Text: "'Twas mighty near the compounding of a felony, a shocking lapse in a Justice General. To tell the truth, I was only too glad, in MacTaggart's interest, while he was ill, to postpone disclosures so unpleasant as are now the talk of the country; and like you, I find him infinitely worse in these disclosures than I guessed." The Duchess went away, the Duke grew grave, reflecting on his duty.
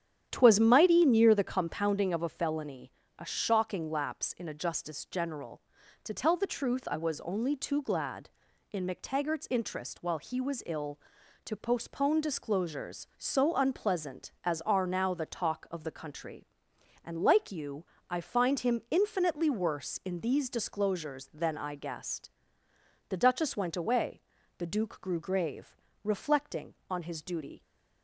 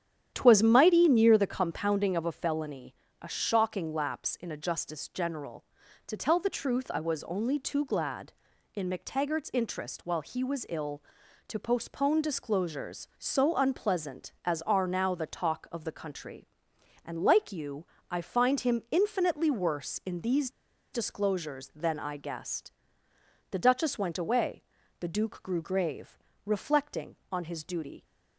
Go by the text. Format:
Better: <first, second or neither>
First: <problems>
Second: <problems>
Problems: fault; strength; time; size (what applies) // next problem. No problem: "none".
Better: first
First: starts louder than the rest; strong; until 1.3 s; 9.5 dB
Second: starts louder than the rest; strong; until 1.3 s; 9.5 dB // pauses between "these" and "disclosures"; at 20.4 s; 0.44 s long